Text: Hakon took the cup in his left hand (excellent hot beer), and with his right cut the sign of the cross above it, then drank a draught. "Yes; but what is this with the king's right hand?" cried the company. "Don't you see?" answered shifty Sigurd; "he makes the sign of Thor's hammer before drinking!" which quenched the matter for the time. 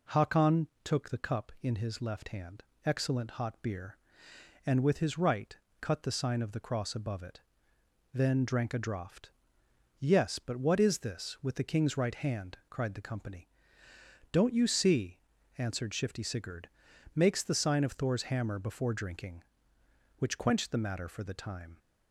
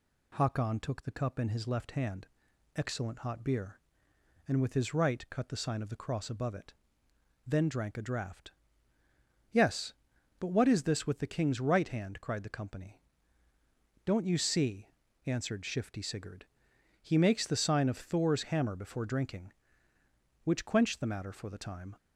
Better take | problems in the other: second | pauses between "Hakon" and "took"; slight; at 0.6 s; 0.16 s long // pauses between "right" and "cut"; slight; at 5.5 s; 0.24 s long // skips "he"; at 16.9 s

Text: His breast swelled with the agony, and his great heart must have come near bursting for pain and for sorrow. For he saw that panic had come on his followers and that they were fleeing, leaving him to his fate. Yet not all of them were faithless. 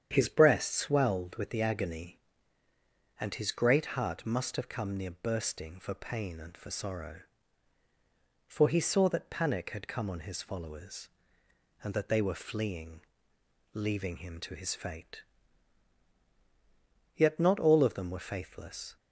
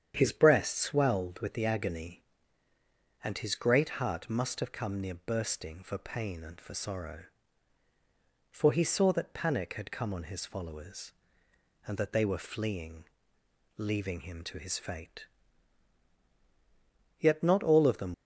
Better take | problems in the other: first | starts louder than the rest; strong; until 1.1 s; 9 dB; strong in the first // stops before "were faithless"; at 18.1 s

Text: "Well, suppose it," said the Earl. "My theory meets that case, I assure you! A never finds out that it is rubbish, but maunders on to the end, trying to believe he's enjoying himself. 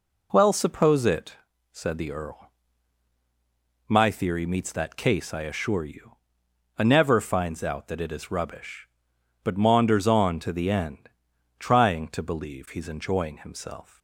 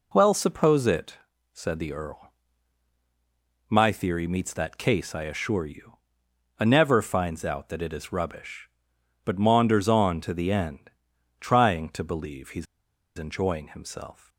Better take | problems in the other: first | pauses between "he's" and "enjoying"; noticeable; at 12.6 s; 0.52 s long

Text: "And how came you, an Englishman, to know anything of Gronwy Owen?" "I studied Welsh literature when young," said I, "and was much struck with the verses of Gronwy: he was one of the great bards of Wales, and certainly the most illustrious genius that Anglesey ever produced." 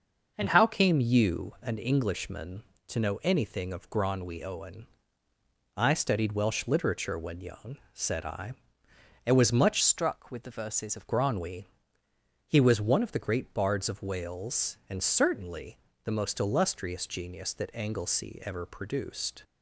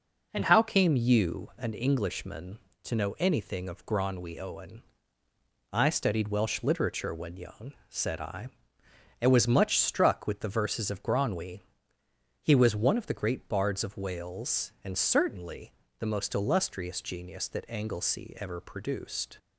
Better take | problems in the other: second | starts louder than the rest; noticeable; until 1.3 s; 6 dB // changes voice from "struck" to "of"; from 9.8 to 11.0 s; 1.2 s long // pauses between "certainly" and "the"; slight; at 15.7 s; 0.26 s long; slight in the second

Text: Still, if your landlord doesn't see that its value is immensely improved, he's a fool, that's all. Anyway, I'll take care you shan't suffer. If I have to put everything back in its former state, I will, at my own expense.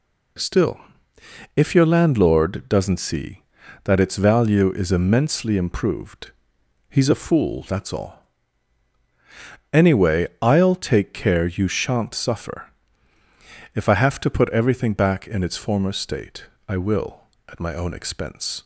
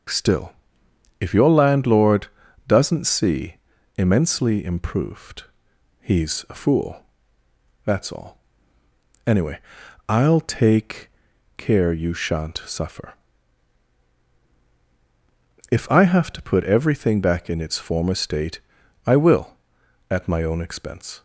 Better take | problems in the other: first | starts louder than the rest; until 1.7 s; 6.5 dB // pauses between "landlord" and "doesn't"; at 2.2 s; 0.38 s long // skips "that its value is"; at 3.7 s // pauses between "take" and "care"; noticeable; at 11.1 s; 0.48 s long

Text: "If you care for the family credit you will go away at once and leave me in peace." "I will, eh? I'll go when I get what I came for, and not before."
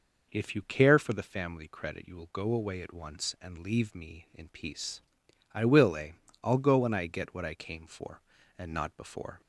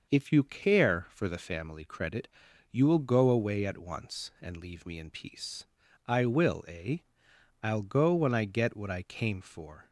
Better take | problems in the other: first | pauses between "credit" and "you"; at 2.2 s; 0.42 s long // stops before "and not before"; at 9.8 s

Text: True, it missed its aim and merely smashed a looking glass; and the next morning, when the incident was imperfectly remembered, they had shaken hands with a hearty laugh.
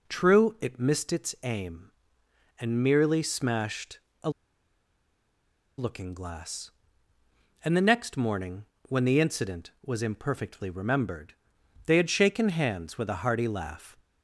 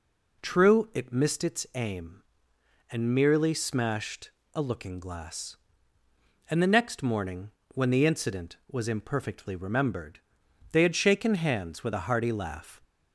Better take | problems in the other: second | pauses between "smashed" and "a"; slight; at 3.9 s; 0.24 s long; slight in the second // pauses between "a" and "looking"; strong; at 4.2 s; 1.4 s long

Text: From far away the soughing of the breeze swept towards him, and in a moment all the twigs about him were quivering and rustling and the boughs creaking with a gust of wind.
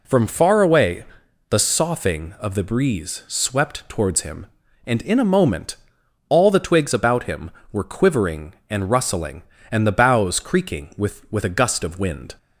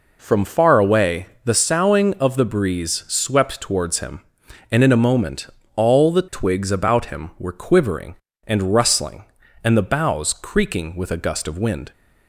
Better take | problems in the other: second | pauses between "away" and "the"; noticeable; at 1.0 s; 0.46 s long; slight in the second // pauses between "moment" and "all"; noticeable; at 5.7 s; 0.52 s long; slight in the second // says "with" twice; at 11.3 s

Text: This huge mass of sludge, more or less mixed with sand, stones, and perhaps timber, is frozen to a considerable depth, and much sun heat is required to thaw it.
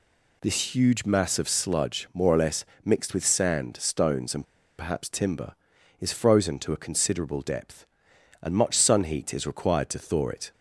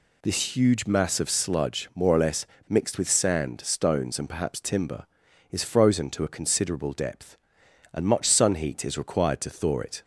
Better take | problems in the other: second | pauses between "less" and "mixed"; slight; at 2.6 s; 0.22 s long; slight in the second // pauses between "and" and "perhaps"; slight; at 4.4 s; 0.33 s long

